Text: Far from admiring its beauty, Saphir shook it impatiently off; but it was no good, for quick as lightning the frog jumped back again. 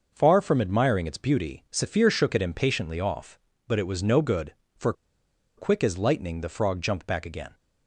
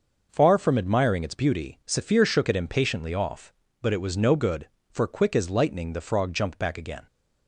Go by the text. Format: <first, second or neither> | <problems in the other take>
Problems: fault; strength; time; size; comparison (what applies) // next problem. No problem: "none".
second | pauses between "for" and "quick"; noticeable; at 4.9 s; 0.65 s long